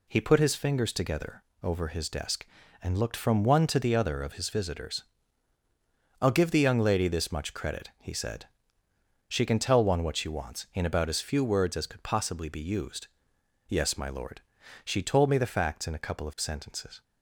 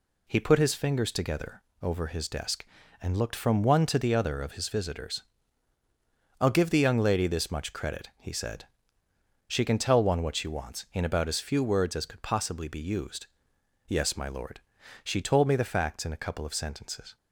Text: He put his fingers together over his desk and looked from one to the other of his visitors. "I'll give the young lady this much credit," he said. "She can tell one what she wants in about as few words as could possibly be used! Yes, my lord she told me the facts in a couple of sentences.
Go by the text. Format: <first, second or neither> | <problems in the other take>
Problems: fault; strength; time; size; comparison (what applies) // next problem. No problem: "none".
neither | pauses between "together" and "over"; slight; the same in both // pauses between "lord" and "she"; the same in both